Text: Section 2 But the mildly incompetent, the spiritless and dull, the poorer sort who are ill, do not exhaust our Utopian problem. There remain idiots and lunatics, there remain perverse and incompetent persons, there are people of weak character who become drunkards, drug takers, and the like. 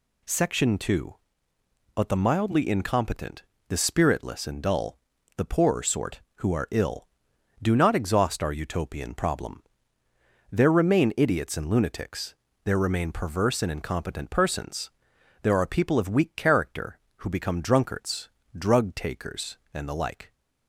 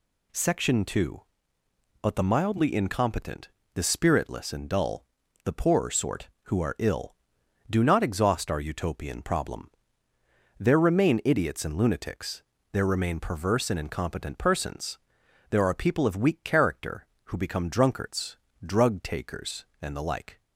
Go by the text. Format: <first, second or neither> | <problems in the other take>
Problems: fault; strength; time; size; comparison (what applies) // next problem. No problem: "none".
neither | none